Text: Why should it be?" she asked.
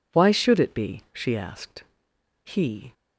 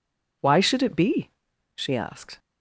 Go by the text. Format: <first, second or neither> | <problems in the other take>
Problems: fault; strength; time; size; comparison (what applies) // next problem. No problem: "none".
second | goes on to say "He"; from 2.4 s on; 0.50 s long